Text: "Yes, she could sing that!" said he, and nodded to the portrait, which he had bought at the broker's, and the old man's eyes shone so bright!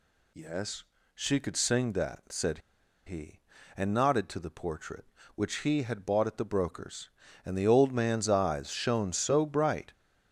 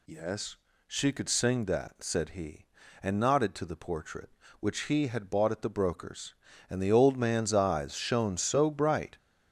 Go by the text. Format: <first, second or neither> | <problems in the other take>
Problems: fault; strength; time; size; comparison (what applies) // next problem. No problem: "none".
second | pauses between "said" and "he"; noticeable; at 2.5 s; 0.47 s long